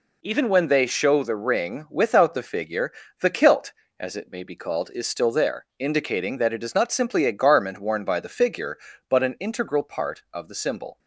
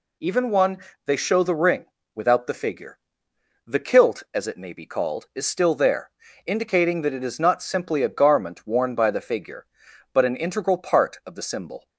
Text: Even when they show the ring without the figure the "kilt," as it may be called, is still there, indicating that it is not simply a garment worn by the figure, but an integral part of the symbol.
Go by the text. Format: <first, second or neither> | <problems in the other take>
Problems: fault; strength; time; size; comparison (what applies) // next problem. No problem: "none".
first | says "one" for "when"; at 0.5 s // pauses between "ring" and "without"; slight; at 1.8 s; 0.28 s long // pauses between "figure" and "the"; noticeable; at 2.9 s; 0.68 s long; slight in the first